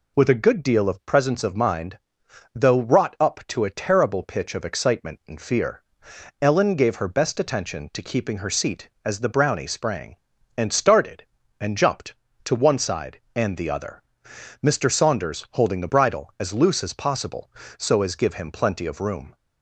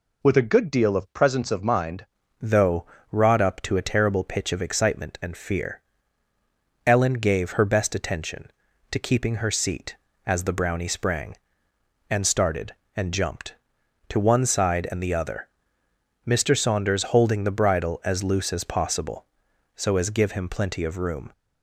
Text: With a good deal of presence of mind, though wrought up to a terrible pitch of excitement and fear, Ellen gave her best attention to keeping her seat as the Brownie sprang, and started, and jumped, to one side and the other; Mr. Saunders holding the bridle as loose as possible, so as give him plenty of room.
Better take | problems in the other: first | changes voice at "though"; from 2.3 s on; 19.0 s long // pauses between "though" and "wrought"; slight; at 2.8 s; 0.24 s long

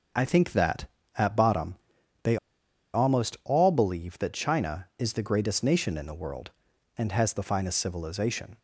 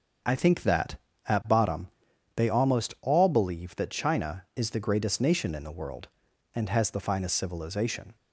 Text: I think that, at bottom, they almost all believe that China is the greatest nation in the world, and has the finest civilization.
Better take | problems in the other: second | starts louder than the rest; until 1.4 s; 6.5 dB; also in the second // pauses between "they" and "almost"; noticeable; at 2.3 s; 0.57 s long

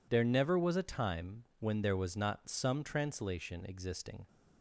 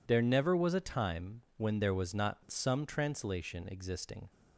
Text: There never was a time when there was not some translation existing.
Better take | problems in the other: neither | none

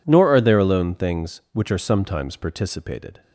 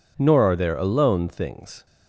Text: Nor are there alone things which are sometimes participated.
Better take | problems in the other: first | stops before "which are sometimes participated"; at 1.8 s

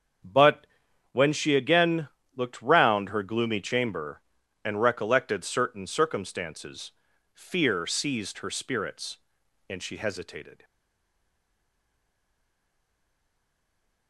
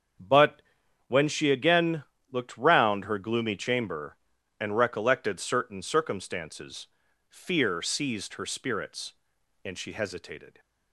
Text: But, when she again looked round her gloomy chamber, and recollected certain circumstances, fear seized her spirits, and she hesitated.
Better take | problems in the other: second | starts louder than the rest; until 1.6 s; 7 dB; also in the second // pauses between "again" and "looked"; slight; at 2.0 s; 0.28 s long; slight in the second // stays silent after the last word; strong; from 10.6 s on; 3.4 s long

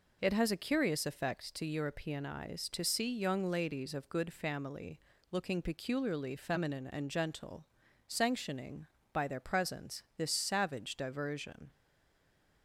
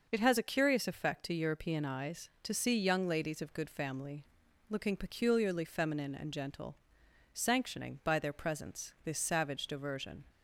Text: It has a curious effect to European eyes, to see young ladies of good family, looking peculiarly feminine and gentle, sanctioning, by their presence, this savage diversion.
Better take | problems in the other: second | stays silent after the last word; slight; from 11.7 s on; 0.9 s long

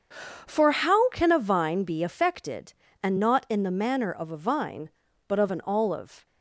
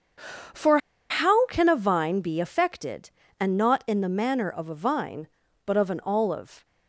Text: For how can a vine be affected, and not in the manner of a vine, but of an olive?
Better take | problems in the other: first | starts louder than the rest; until 1.8 s; 7 dB; also in the first // pauses between "For" and "how"; slight; at 0.7 s; 0.31 s long

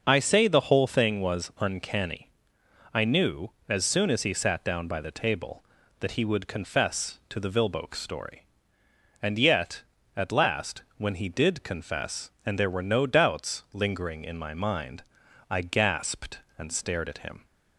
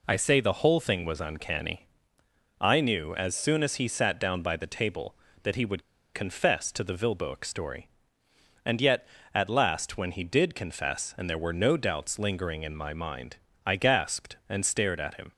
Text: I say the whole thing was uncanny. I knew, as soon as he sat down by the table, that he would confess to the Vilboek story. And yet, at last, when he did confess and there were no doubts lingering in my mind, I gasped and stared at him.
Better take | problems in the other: first | pauses between "would" and "confess"; slight; at 5.8 s; 0.31 s long

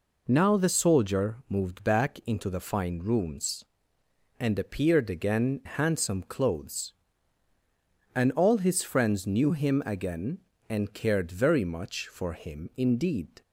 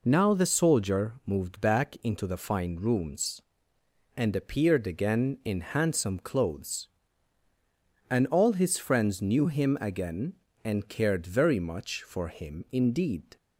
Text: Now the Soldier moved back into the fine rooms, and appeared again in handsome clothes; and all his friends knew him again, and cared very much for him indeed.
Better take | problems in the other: second | skips "in"; at 5.6 s

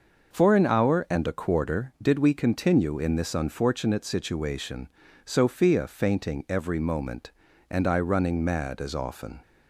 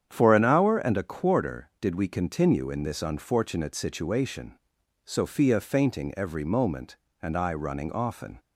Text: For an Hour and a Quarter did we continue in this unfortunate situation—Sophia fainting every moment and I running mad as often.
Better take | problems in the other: first | starts louder than the rest; strong; until 1.1 s; 8.5 dB; noticeable in the first // skips "mad as"; at 7.9 s

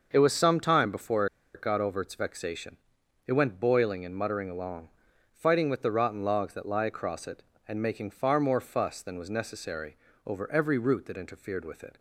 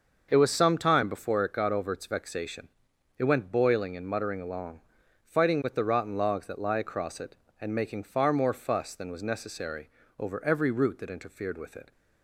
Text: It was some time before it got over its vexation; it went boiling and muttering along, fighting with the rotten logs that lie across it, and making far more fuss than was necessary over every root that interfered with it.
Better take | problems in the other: second | starts louder than the rest; until 1.1 s; 6 dB; also in the second // pauses between "before" and "it"; slight; at 1.2 s; 0.28 s long // pauses between "necessary" and "over"; slight; at 9.9 s; 0.28 s long; slight in the second

